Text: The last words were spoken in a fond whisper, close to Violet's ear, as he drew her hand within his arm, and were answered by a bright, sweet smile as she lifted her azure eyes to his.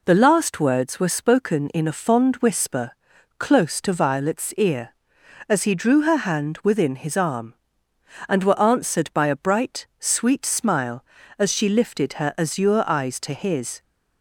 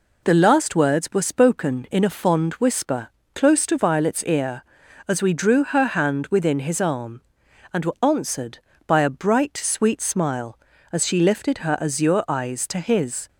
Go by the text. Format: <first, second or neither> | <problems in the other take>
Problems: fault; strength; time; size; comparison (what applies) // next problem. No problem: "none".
first | says "we" for "he"; at 5.2 s